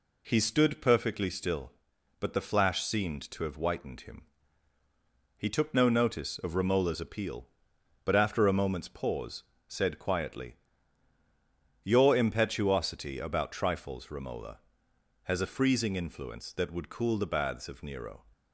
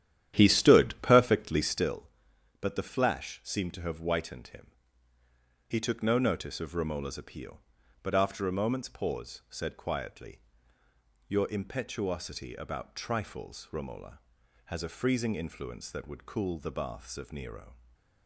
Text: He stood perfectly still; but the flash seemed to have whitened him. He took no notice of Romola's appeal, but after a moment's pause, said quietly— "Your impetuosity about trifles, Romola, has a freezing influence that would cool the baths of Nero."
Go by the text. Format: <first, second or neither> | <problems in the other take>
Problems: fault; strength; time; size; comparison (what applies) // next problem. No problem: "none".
first | starts louder than the rest; strong; until 1.9 s; 11 dB // stays silent after the last word; slight; from 17.7 s on; 0.5 s long